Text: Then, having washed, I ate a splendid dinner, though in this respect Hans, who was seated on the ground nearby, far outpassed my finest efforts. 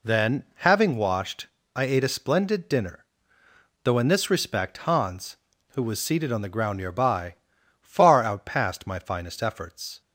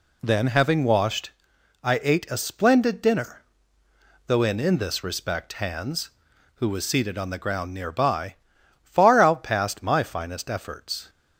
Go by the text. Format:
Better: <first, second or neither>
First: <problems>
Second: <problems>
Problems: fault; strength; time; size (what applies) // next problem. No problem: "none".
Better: first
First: none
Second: says "in" twice; at 4.5 s